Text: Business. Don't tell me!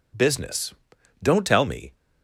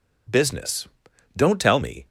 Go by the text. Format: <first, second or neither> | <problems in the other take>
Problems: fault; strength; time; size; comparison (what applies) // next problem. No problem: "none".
neither | none